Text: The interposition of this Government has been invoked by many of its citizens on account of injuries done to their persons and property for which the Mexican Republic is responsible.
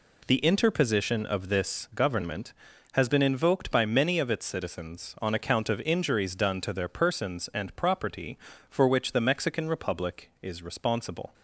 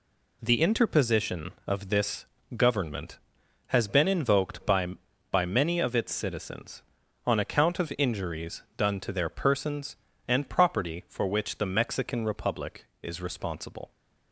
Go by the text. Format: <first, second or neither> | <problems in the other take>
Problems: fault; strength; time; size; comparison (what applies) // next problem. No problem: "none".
first | pauses between "this" and "Government"; slight; at 2.2 s; 0.30 s long // says "by" twice; at 5.2 s